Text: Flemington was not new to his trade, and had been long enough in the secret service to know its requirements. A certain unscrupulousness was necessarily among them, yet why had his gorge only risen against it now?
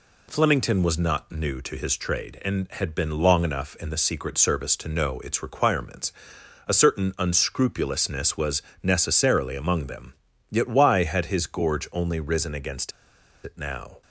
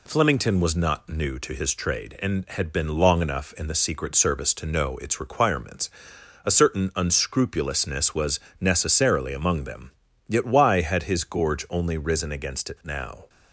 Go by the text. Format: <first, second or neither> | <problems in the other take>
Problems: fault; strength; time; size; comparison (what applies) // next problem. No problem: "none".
second | pauses between "was" and "necessarily"; slight; at 8.6 s; 0.22 s long; slight in the second // pauses between "against" and "it"; noticeable; at 12.9 s; 0.54 s long